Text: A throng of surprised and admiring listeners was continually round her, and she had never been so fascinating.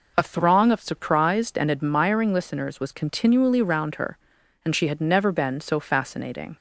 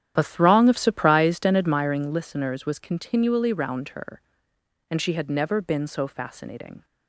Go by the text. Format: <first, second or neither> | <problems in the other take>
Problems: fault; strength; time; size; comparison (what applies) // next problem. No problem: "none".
first | starts louder than the rest; strong; until 1.8 s; 10.5 dB